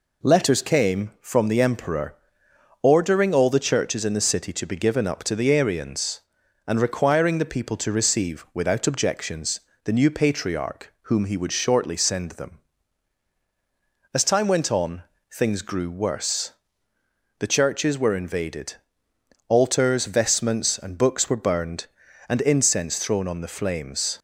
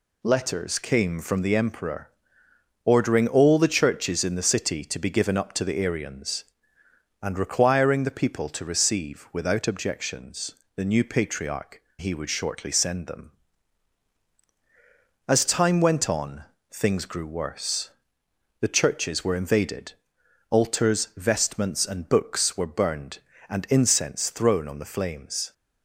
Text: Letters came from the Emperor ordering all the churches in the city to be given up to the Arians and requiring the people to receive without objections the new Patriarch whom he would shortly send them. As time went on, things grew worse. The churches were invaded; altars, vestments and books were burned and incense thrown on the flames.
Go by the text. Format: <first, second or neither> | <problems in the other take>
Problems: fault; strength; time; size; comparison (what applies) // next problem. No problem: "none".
first | pauses between "Emperor" and "ordering"; noticeable; at 2.0 s; 0.74 s long; noticeable in the first // pauses between "objections" and "the"; slight; at 10.5 s; 0.18 s long; slight in the first // skips "whom"; at 11.8 s